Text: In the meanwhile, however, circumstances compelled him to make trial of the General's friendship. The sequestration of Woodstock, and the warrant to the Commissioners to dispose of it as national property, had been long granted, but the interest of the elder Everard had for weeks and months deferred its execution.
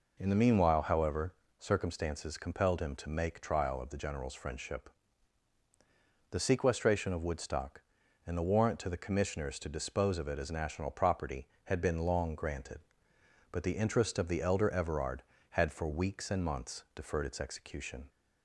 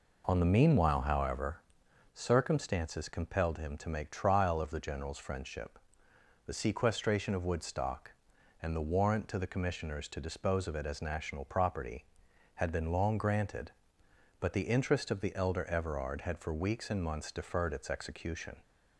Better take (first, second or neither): first